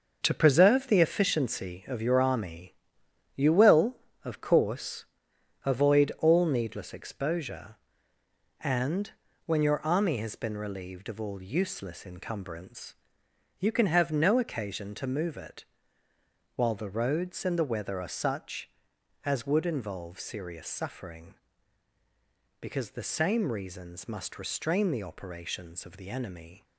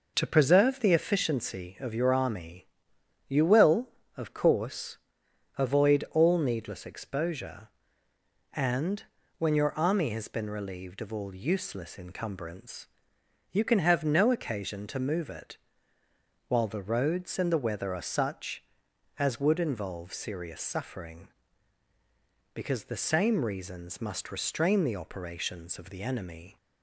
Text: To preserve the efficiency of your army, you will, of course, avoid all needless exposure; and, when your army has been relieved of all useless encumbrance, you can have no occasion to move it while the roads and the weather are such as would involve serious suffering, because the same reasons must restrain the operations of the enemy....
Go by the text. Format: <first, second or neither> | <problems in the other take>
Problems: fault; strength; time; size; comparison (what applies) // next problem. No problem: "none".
second | gets quieter; strong; throughout; 8 dB // pauses between "it" and "while"; noticeable; at 15.6 s; 0.90 s long; noticeable in the second